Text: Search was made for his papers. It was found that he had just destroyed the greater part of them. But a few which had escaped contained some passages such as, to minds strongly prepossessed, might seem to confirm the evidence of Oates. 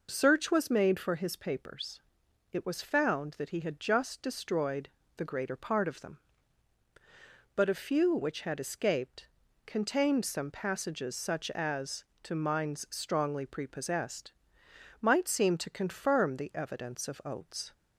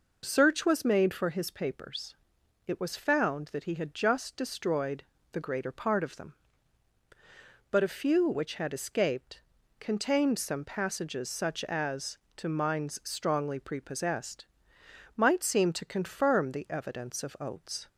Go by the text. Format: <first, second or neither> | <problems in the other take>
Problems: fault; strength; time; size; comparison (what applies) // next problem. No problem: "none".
neither | pauses between "destroyed" and "the"; slight; the same in both // pauses between "escaped" and "contained"; the same in both